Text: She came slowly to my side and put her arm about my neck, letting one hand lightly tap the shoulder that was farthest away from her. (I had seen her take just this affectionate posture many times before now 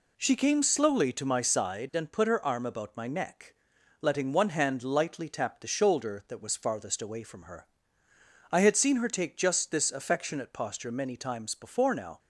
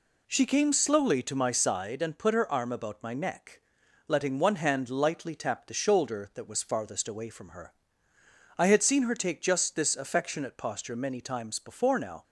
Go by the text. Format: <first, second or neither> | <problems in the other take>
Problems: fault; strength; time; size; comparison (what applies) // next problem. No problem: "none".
neither | none